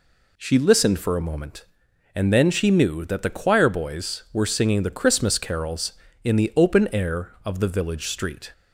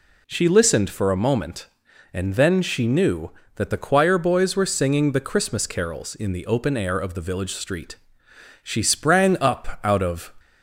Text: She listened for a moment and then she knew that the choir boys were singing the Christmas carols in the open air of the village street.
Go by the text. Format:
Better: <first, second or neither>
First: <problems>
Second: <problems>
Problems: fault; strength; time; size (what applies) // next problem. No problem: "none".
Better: first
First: none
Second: goes on to say "She sprang up out of"; strong; from 8.6 s on; 1.7 s long